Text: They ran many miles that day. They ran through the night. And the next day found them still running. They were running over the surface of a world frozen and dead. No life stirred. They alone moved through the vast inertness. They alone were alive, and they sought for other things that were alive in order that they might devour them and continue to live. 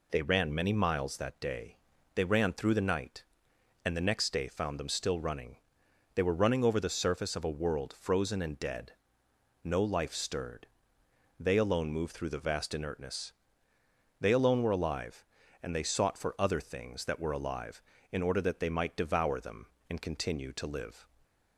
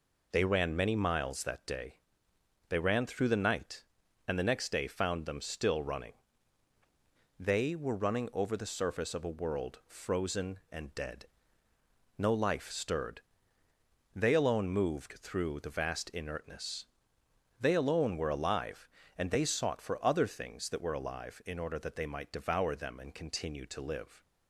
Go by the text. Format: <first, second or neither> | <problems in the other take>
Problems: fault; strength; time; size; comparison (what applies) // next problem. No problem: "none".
neither | none